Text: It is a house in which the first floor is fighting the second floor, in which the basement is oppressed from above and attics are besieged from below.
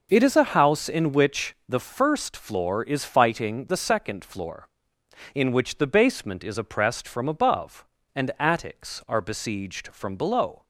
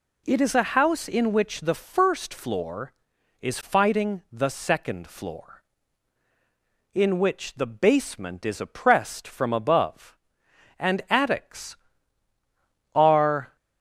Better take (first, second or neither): first